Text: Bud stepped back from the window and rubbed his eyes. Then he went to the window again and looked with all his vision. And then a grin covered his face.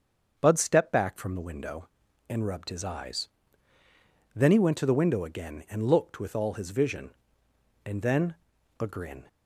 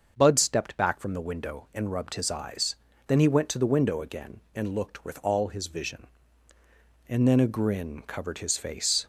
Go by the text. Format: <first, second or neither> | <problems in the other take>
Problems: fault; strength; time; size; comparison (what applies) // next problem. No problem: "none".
second | starts louder than the rest; until 1.3 s; 6.5 dB; also in the second // pauses between "then" and "a"; at 8.3 s; 0.44 s long // stops before "covered his face"; at 9.2 s